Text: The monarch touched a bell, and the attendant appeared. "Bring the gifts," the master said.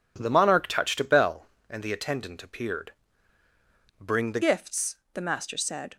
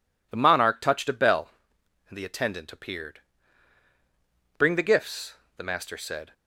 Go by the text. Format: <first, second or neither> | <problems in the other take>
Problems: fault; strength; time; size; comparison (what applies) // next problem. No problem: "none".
second | changes voice at "gifts"; from 4.4 s on; 1.5 s long